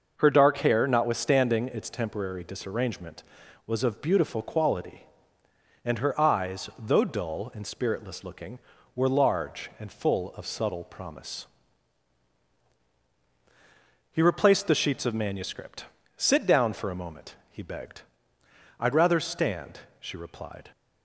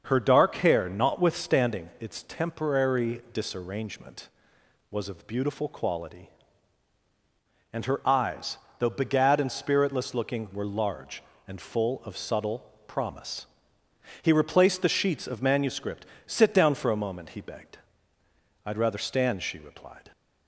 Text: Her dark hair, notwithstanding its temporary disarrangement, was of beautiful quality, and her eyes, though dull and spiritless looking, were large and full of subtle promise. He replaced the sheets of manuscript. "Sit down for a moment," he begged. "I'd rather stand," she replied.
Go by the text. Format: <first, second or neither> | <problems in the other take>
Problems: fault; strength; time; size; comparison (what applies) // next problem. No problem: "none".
first | starts louder than the rest; until 1.0 s; 6.5 dB; noticeable in the first // says "begad" for "dull"; at 8.9 s // pauses between "subtle" and "promise"; slight; at 12.6 s; 0.16 s long